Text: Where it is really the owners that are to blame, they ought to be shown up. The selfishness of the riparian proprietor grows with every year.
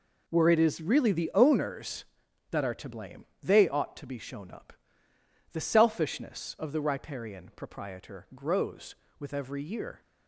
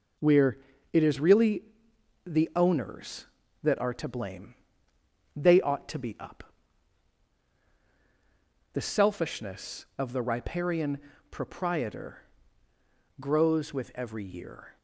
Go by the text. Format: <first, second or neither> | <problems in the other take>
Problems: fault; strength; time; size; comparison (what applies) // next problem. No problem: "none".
first | pauses between "Where" and "it"; slight; at 0.5 s; 0.36 s long // pauses between "really" and "the"; noticeable; at 1.6 s; 0.62 s long // skips "shown"; at 6.1 s // pauses between "riparian" and "proprietor"; slight; at 10.9 s; 0.32 s long // pauses between "proprietor" and "grows"; noticeable; at 12.2 s; 0.96 s long